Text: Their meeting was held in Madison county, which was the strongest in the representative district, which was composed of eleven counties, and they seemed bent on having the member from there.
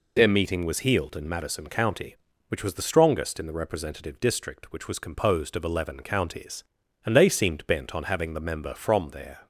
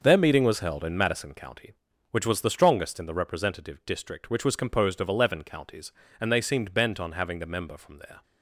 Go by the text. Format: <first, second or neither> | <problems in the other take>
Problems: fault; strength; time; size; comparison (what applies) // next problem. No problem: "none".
second | says "healed" for "held"; at 0.7 s